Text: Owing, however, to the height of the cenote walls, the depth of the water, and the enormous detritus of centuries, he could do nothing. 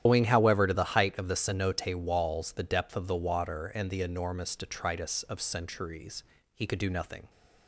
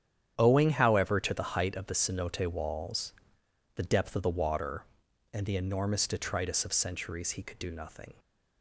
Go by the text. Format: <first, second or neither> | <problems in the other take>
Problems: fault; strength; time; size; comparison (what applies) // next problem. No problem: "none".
second | loses the start of "Owing"; at 0.0 s; 95 ms // starts louder than the rest; strong; until 1.0 s; 11 dB; strong in the second